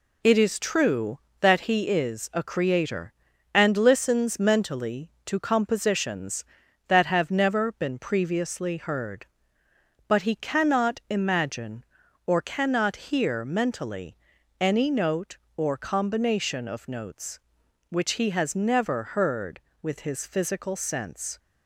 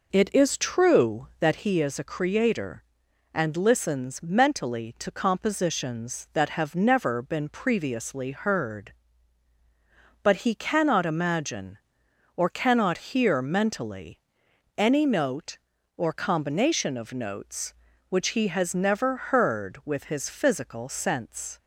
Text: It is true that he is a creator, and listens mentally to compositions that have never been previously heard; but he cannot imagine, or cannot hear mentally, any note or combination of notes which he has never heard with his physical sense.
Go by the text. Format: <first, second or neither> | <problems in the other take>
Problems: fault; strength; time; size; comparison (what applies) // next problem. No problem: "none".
first | starts louder than the rest; noticeable; until 1.5 s; 5 dB